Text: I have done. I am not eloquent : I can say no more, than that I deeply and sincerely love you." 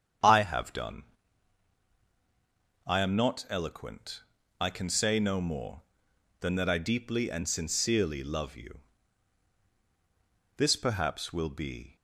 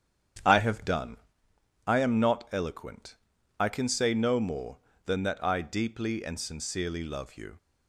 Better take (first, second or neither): second